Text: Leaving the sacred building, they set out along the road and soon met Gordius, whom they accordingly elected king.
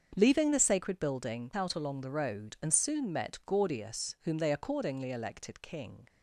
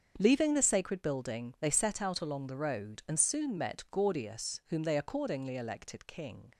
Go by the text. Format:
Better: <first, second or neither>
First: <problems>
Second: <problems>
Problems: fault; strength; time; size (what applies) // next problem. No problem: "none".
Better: second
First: starts louder than the rest; until 1.1 s; 7 dB // skips "they set"; at 1.5 s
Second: starts louder than the rest; until 1.1 s; 7 dB